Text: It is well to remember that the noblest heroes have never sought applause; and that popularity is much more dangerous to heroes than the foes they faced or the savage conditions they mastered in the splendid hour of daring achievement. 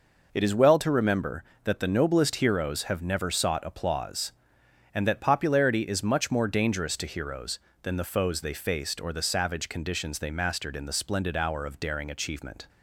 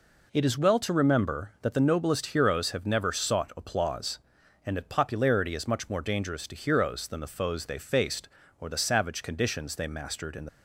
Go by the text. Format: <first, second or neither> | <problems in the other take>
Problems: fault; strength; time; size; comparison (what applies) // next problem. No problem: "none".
first | stops before "splendid hour of daring achievement"; at 10.4 s